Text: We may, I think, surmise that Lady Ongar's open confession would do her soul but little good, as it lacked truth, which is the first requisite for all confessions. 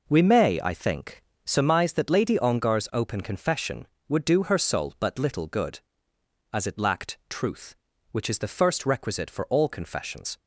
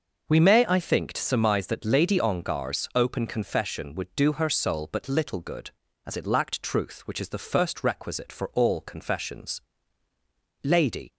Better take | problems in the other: first | goes on to say "Lady"; from 10.6 s on; 0.52 s long

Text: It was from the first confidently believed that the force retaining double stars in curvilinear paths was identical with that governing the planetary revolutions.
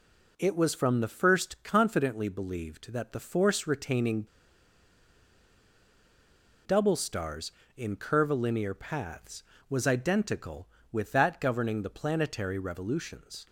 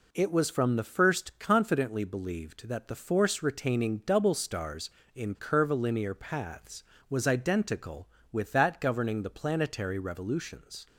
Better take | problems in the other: second | pauses between "retaining" and "double"; strong; at 4.2 s; 2.3 s long

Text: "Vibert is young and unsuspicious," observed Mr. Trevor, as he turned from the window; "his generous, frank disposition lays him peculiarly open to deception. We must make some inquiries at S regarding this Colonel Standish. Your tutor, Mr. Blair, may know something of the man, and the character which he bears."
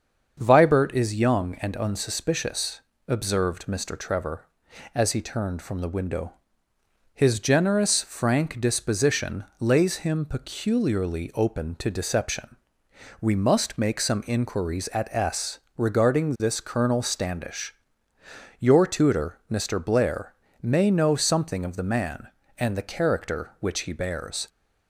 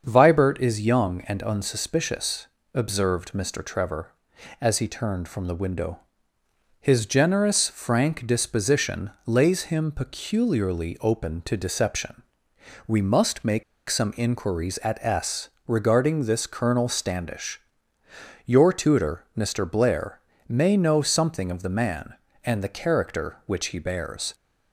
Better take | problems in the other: first | starts louder than the rest; until 1.0 s; 7 dB; also in the first // pauses between "make" and "some"; slight; at 13.6 s; 0.24 s long // pauses between "S" and "regarding"; slight; at 15.4 s; 0.18 s long; slight in the first

